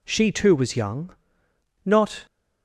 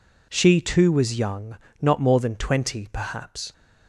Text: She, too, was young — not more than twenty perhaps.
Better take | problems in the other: second | stops before "more than twenty perhaps"; at 2.2 s

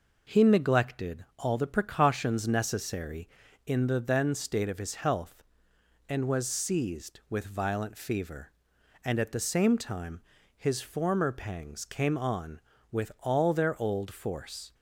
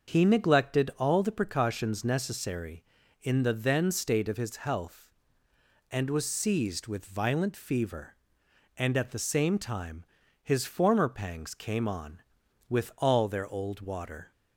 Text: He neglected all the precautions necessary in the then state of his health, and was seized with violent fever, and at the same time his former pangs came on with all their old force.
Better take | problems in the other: first | starts louder than the rest; until 1.1 s; 6.5 dB // pauses between "time" and "his"; slight; at 10.0 s; 0.36 s long; slight in the first // says "water" for "force"; at 13.8 s

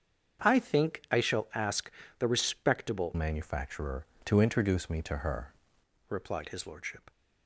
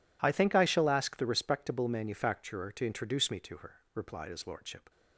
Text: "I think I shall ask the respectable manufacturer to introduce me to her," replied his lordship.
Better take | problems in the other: second | starts louder than the rest; strong; until 1.5 s; 7.5 dB // pauses between "ask" and "the"; slight; at 1.9 s; 0.28 s long // changes voice from "manufacturer" to "her"; from 3.1 to 5.5 s; 2.4 s long

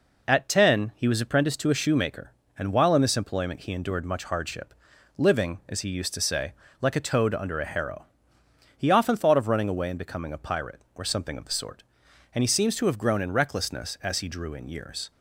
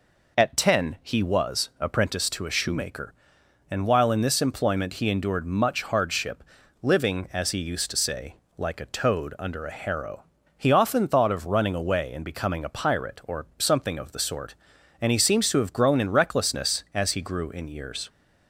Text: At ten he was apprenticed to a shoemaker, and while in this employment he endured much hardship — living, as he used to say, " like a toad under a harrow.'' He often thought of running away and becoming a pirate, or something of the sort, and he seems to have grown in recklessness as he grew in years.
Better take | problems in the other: second | says "drew" for "grew"; at 14.2 s

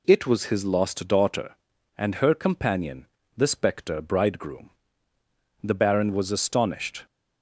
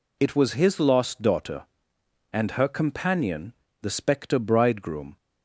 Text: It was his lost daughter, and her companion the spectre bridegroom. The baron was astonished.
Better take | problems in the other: first | pauses between "companion" and "the"; slight; at 3.5 s; 0.30 s long; slight in the first // stops before "The baron was astonished"; at 5.1 s

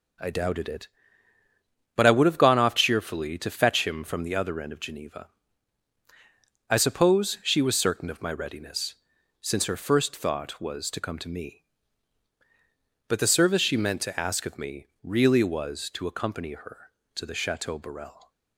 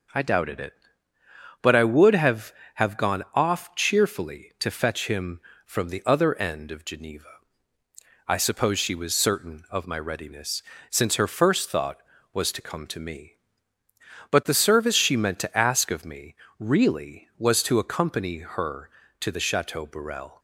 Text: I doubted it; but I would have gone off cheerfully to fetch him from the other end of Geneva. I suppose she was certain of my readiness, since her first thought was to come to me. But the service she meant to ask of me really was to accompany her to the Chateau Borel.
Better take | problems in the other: first | says "have" twice; at 2.7 s // pauses between "me" and "really"; slight; at 16.3 s; 0.24 s long; slight in the first

